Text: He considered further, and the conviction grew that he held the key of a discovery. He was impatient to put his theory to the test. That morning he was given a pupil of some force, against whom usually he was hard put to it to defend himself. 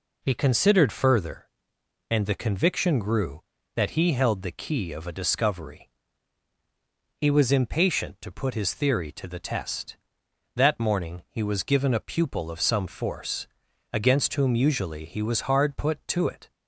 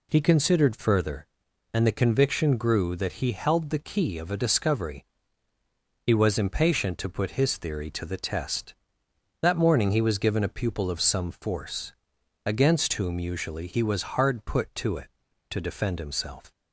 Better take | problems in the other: second | stops before "to defend himself"; at 16.5 s

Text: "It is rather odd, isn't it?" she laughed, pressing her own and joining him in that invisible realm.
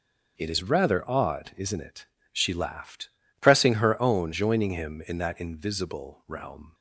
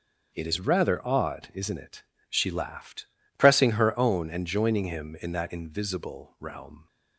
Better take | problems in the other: second | skips "and"; at 4.3 s

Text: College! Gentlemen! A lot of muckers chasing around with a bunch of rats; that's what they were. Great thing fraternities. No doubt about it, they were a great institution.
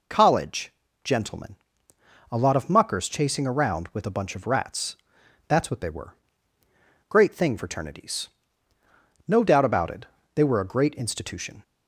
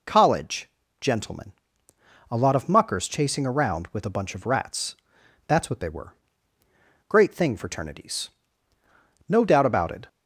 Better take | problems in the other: first | stops before "they were a great institution"; at 10.0 s

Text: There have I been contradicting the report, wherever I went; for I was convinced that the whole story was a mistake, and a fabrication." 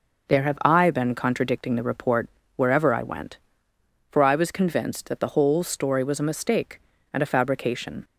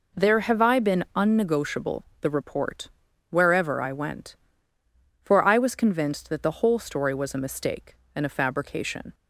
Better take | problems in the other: first | says "unnegotiable" for "contradicting"; at 1.1 s

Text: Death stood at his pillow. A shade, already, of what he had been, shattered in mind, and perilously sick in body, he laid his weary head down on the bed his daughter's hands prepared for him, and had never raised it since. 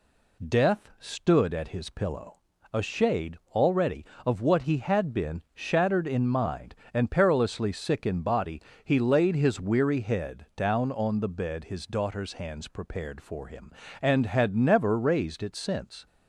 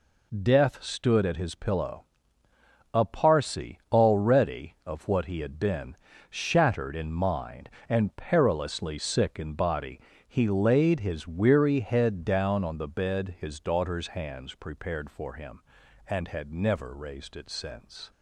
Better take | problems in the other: first | says "parsi" for "shade"; at 3.0 s

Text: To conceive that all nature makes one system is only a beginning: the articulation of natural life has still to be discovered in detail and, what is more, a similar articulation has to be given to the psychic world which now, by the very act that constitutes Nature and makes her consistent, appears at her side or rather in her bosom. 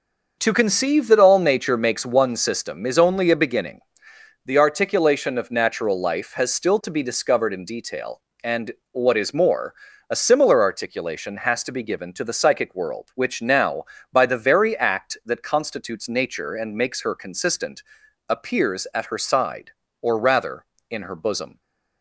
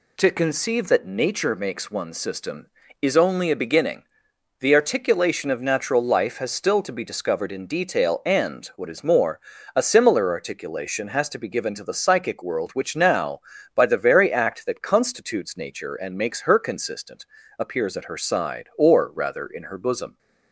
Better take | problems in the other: first | skips "all"; at 1.0 s

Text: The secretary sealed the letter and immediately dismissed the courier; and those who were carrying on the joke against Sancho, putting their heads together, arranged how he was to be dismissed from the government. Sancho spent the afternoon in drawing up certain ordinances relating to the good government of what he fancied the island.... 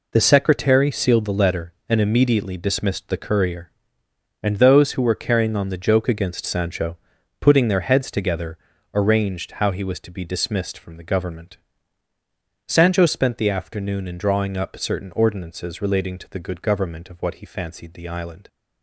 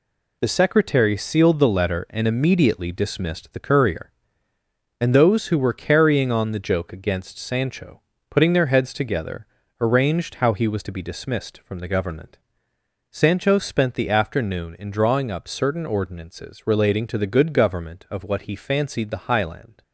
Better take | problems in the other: first | says "highland" for "island"; at 19.3 s

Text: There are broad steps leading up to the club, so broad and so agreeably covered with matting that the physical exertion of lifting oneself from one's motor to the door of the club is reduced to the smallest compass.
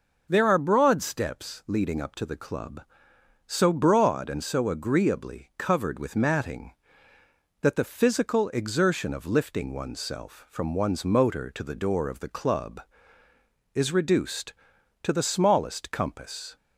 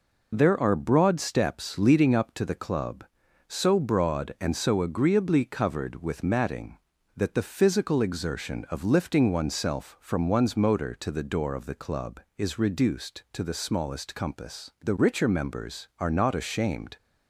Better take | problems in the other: first | goes on to say "The richer members are not ashamed"; strong; from 14.8 s on; 2.1 s long

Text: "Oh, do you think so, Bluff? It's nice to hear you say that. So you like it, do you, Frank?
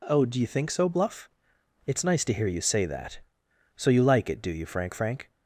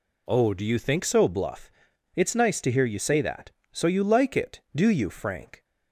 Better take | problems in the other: second | says "Frank" twice; at 4.9 s

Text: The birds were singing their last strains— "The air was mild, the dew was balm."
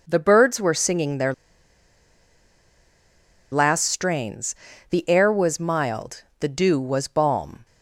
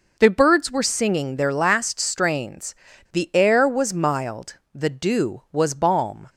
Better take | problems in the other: second | pauses between "their" and "last"; strong; at 1.3 s; 2.2 s long

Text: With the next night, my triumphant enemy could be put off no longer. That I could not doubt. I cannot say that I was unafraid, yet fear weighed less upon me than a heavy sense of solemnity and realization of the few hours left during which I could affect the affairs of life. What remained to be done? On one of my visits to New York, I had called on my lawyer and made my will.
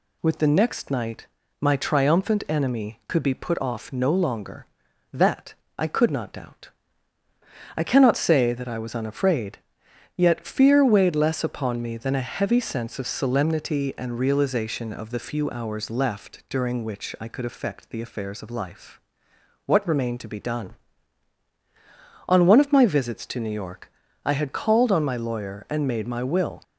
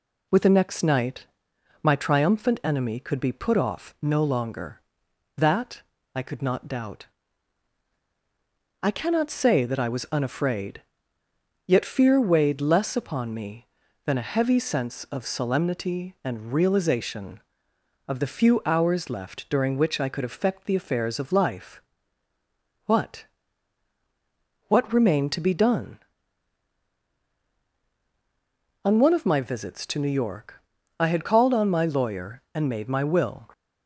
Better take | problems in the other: first | pauses between "That" and "I"; slight; at 5.8 s; 0.32 s long; slight in the first // says "What" twice; at 24.6 s

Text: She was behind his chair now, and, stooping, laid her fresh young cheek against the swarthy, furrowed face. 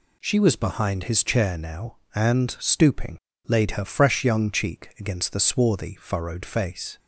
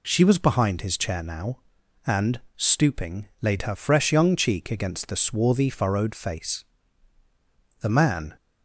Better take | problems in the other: first | goes on to say "The man"; from 7.7 s on; 0.56 s long

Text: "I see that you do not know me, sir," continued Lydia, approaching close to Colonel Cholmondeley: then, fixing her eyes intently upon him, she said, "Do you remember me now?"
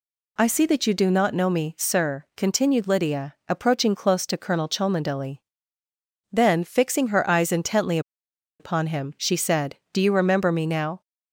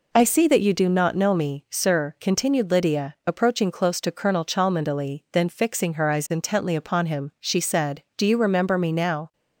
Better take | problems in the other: second | pauses between "intently" and "upon"; noticeable; at 7.9 s; 0.60 s long

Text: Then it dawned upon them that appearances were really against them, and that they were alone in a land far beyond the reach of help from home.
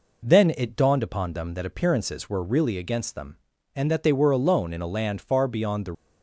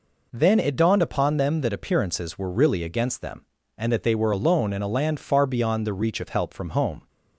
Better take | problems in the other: second | stops before "reach of help from home"; at 5.9 s

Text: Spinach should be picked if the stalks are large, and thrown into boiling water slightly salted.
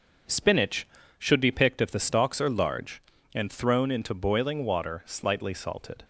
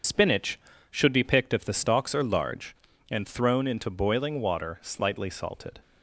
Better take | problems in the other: first | loses the start of "Spinach"; at 0.0 s; 45 ms // starts louder than the rest; until 1.3 s; 6.5 dB

